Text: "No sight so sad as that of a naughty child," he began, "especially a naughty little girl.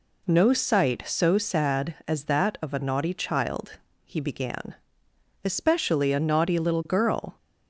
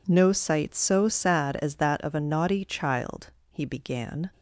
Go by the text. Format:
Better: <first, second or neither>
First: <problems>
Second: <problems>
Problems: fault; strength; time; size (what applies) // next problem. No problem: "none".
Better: first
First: none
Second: stops before "especially a naughty little girl"; at 4.3 s